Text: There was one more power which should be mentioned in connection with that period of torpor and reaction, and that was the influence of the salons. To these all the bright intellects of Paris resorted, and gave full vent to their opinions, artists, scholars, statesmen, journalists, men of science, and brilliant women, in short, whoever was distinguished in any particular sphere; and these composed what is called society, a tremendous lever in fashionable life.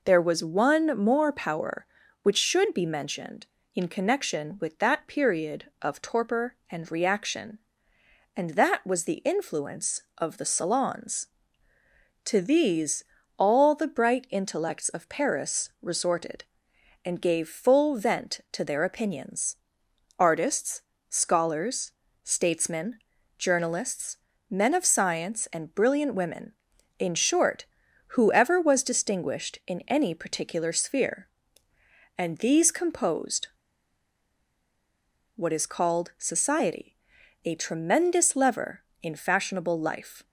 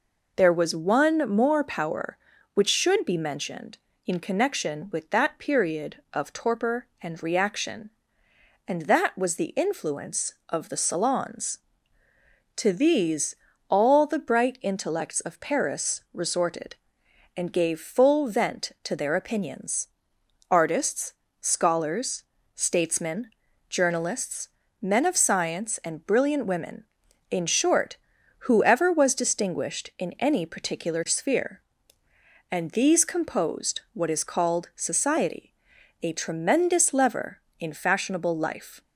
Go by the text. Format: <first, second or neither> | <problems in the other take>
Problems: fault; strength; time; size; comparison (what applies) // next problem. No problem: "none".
second | pauses between "these" and "all"; slight; at 13.0 s; 0.34 s long; slight in the second // pauses between "composed" and "what"; strong; at 33.4 s; 1.8 s long